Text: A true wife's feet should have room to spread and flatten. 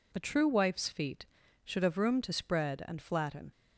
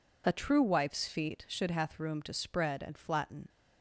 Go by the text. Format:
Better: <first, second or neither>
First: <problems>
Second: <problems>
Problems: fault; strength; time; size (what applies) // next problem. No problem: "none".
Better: first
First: none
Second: says "hath" for "have"; at 1.7 s